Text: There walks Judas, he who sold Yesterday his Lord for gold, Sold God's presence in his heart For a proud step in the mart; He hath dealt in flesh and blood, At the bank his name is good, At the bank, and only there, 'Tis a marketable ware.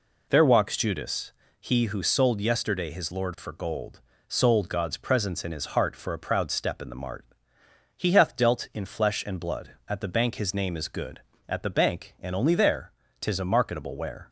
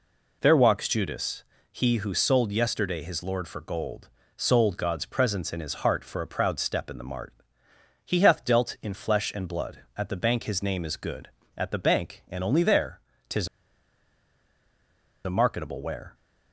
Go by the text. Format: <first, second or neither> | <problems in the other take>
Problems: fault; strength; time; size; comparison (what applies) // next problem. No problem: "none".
first | pauses between "Tis" and "a"; strong; at 13.4 s; 1.7 s long